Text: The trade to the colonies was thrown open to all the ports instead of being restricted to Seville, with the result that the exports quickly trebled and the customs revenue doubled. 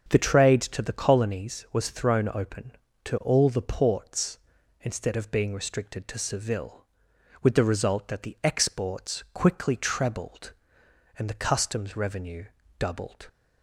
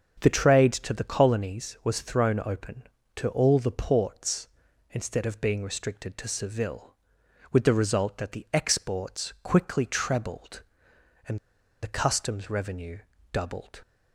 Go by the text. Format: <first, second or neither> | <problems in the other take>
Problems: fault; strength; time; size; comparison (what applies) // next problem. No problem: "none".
first | starts louder than the rest; until 1.2 s; 6.5 dB; also in the first // pauses between "and" and "the"; at 11.3 s; 0.44 s long // pauses between "revenue" and "doubled"; slight; at 12.9 s; 0.34 s long; slight in the first